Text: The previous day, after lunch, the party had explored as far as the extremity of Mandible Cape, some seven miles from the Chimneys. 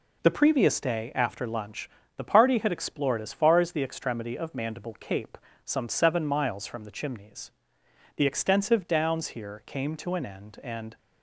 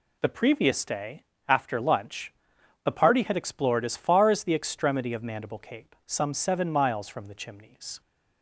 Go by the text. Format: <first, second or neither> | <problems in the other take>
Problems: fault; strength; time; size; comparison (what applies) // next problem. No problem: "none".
second | goes on to say "The extensive downs here came to an end and"; strong; from 8.1 s on; 2.7 s long